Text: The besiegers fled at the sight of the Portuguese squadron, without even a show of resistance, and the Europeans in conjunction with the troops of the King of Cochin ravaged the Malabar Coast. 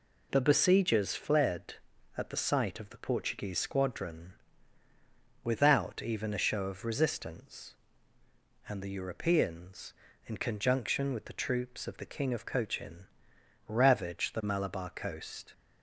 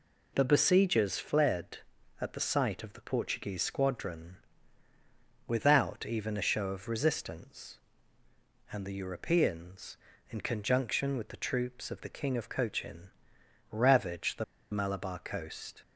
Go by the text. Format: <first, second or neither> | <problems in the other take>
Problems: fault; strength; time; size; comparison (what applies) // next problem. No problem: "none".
first | pauses between "Cochin" and "ravaged"; noticeable; at 13.1 s; 0.60 s long; noticeable in the first // pauses between "the" and "Malabar"; slight; at 14.4 s; 0.29 s long